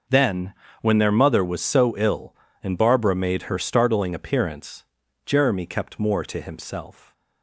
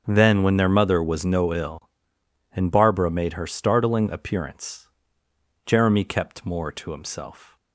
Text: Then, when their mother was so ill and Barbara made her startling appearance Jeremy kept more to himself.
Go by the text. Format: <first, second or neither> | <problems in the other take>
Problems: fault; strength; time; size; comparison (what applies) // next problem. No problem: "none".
first | starts louder than the rest; until 1.0 s; 6.5 dB // says "no" for "so"; at 1.2 s // pauses between "appearance" and "Jeremy"; noticeable; at 4.8 s; 0.78 s long; also in the first